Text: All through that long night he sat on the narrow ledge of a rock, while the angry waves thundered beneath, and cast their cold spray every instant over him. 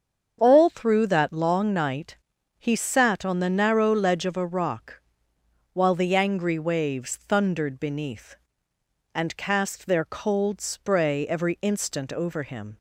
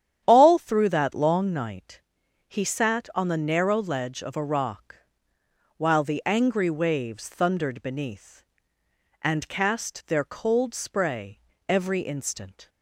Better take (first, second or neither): first